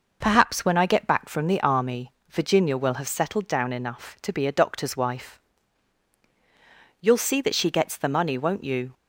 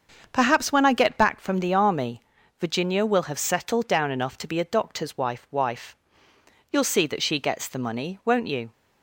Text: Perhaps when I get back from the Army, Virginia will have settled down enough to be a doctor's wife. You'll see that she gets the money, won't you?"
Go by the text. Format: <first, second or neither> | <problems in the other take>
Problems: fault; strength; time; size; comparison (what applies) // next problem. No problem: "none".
first | starts louder than the rest; until 1.3 s; 6.5 dB // says "wife" twice; at 5.5 s